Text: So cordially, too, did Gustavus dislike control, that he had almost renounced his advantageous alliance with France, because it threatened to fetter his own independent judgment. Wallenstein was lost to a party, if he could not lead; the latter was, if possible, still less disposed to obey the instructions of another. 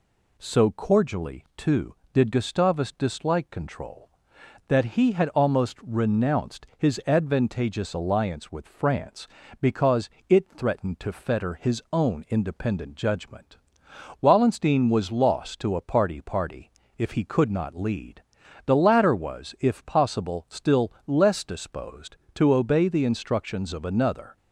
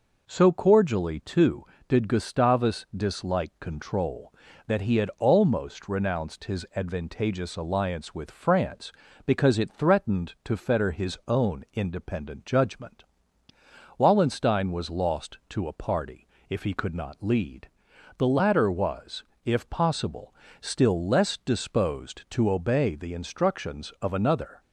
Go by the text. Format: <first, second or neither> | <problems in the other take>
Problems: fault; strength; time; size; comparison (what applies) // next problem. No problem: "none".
second | pauses between "because" and "it"; slight; at 10.0 s; 0.20 s long // says "party" twice; at 16.2 s